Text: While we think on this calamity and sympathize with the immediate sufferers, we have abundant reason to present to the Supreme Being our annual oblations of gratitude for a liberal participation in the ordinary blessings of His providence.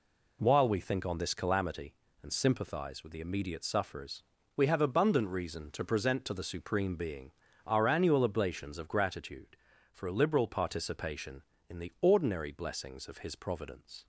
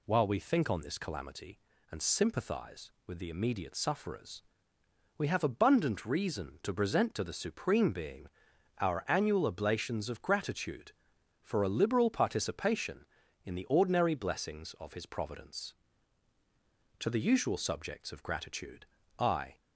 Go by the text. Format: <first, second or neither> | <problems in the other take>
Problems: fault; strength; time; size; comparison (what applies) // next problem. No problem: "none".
first | pauses between "Being" and "our"; noticeable; at 8.2 s; 0.52 s long; slight in the first // goes on to say "To the usual subjects of gratitude I"; strong; from 16.9 s on; 2.5 s long